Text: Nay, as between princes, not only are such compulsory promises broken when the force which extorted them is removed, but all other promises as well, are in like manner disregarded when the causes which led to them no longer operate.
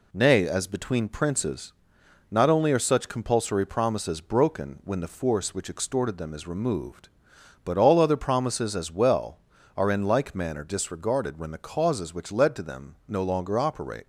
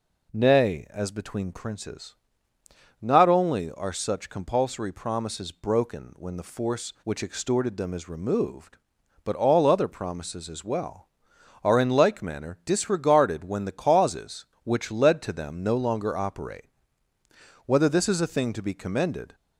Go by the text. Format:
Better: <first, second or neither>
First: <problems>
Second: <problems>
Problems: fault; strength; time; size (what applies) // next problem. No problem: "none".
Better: first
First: none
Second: goes on to say "Whether this is a thing to be commended"; strong; from 17.6 s on; 1.7 s long